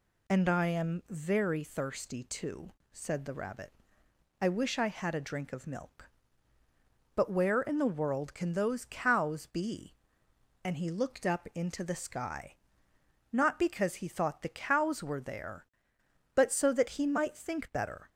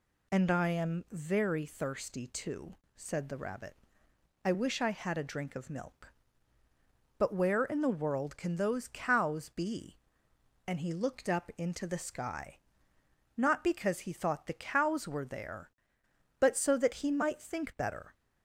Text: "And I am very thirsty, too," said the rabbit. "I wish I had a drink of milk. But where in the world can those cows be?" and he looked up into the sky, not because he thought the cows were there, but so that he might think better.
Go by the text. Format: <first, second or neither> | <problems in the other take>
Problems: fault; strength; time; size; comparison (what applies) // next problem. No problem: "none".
neither | none